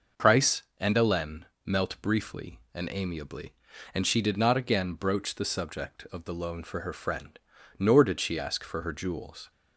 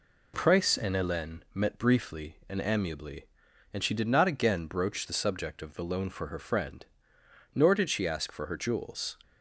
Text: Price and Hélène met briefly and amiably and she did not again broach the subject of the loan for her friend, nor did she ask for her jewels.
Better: second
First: starts louder than the rest; noticeable; until 1.3 s; 6 dB // says "melt" for "met"; at 1.6 s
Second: none

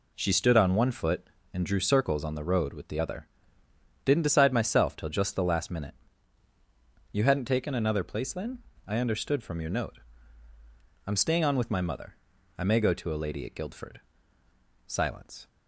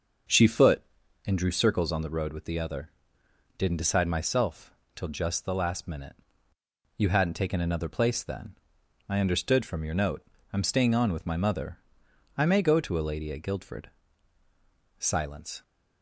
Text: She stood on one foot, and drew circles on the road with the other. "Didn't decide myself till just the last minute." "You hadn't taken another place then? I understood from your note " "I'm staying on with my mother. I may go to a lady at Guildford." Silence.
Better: first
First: none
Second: starts louder than the rest; until 1.7 s; 6.5 dB // skips "stood on one"; at 0.4 s // pauses between "myself" and "till"; slight; at 4.7 s; 0.20 s long

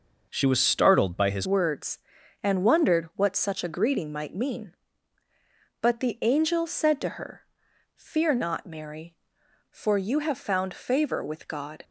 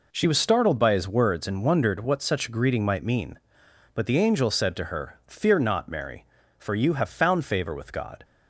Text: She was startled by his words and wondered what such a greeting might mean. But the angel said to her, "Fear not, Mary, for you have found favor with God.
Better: second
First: changes voice at "words"; from 1.4 s on; 10.4 s long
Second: none

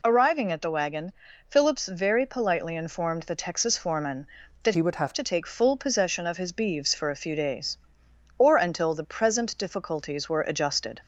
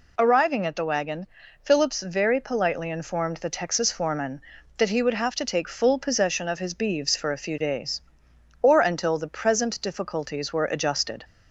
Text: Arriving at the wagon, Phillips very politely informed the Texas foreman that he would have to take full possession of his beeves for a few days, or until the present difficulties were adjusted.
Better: second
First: changes voice from "he" to "have"; from 4.7 to 5.1 s; 0.4 s long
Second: none

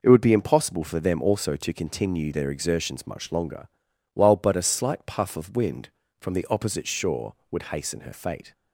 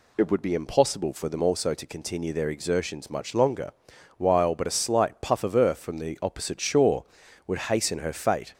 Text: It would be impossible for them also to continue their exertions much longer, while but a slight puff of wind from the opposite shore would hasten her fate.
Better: first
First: none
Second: says "earth" for "wind"; at 5.5 s

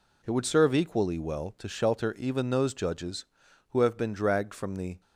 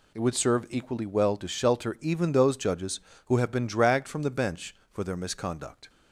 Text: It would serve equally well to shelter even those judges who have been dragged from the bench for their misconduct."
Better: second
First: stops before "bench for their misconduct"; at 5.0 s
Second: none

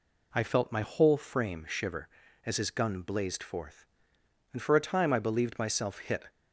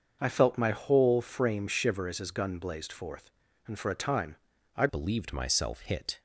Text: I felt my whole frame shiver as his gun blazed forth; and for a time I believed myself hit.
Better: first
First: none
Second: starts louder than the rest; until 1.2 s; 6.5 dB // pauses between "time" and "I"; at 4.3 s; 0.40 s long // changes voice at "believed"; from 4.8 s on; 1.4 s long

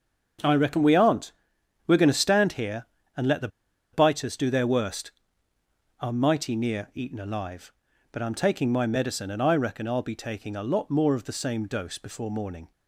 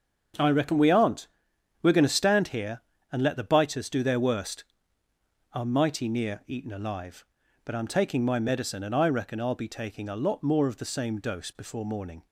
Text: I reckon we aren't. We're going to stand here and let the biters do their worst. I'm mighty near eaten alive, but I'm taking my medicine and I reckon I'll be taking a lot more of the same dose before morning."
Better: second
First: starts louder than the rest; until 1.9 s; 7 dB // pauses between "the" and "biters"; at 3.4 s; 0.45 s long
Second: starts louder than the rest; until 1.9 s; 7 dB

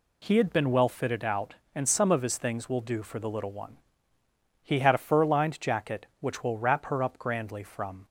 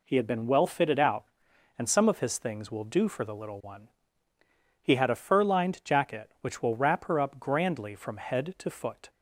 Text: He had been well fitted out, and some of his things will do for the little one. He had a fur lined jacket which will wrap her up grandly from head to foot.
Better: second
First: stops before "head to foot"; at 8.0 s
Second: none

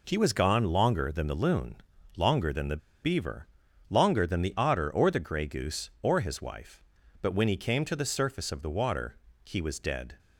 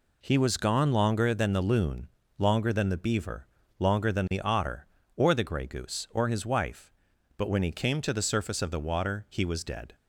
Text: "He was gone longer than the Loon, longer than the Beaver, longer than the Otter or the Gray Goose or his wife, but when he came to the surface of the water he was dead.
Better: second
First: pauses between "the" and "Beaver"; slight; at 2.7 s; 0.25 s long // pauses between "water" and "he"; slight; at 9.1 s; 0.30 s long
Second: none

